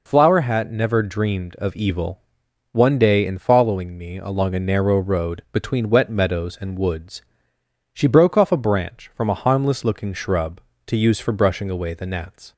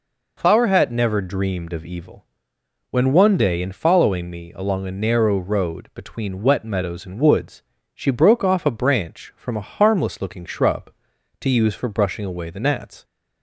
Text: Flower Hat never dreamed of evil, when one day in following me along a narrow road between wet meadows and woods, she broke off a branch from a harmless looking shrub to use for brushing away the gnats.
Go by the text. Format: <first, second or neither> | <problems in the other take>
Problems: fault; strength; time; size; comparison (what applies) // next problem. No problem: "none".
second | skips "when"; at 2.4 s